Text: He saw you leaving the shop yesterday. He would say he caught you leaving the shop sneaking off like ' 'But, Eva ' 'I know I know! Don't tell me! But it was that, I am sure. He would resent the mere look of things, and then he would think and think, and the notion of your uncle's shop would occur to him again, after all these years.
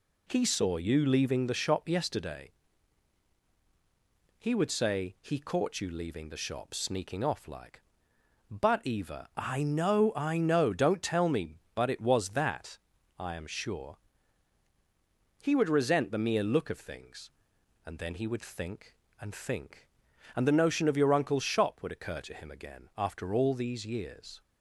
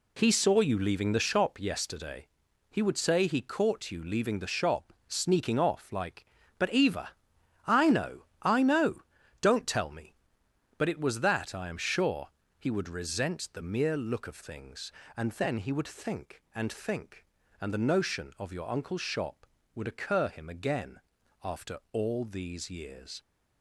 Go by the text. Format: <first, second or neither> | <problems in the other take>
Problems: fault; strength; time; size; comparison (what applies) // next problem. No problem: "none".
first | pauses between "shop" and "sneaking"; slight; at 4.9 s; 0.16 s long // pauses between "know" and "I"; slight; at 8.2 s; 0.16 s long // skips "to"; at 20.2 s